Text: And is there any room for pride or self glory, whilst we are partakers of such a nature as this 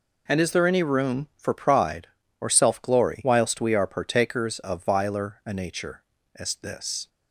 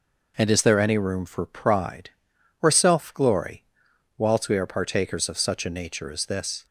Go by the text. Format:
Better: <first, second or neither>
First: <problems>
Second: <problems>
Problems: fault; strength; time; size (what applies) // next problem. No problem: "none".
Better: second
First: says "viler" for "such"; at 4.8 s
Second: none